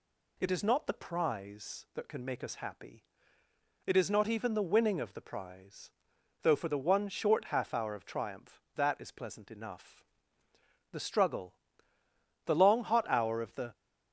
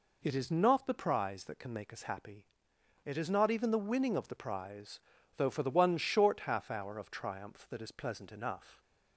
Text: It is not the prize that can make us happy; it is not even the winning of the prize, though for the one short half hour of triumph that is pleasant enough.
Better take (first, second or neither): second